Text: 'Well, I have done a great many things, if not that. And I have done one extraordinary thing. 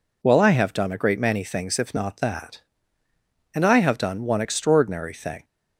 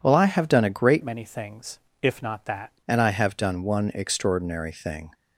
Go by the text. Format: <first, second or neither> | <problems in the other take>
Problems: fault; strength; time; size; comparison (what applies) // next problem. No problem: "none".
first | changes voice from "many" to "that"; from 1.0 to 2.7 s; 1.7 s long